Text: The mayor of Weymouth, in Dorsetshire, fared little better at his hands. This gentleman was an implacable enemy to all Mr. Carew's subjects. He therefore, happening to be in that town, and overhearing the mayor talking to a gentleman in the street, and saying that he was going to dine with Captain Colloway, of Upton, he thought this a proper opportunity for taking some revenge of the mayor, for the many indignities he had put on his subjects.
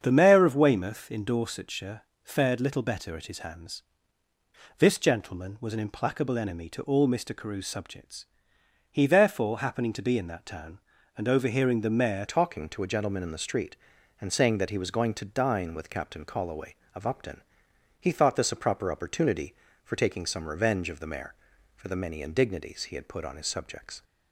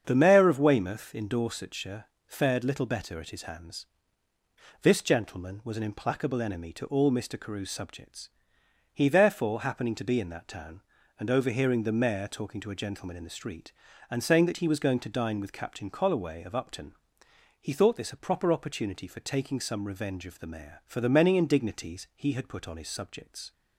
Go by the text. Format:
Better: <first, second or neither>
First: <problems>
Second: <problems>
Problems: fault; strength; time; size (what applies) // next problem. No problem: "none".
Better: second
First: starts louder than the rest; strong; until 1.0 s; 7.5 dB // changes voice at "talking"; from 12.2 s on; 11.8 s long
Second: starts louder than the rest; strong; until 1.0 s; 7.5 dB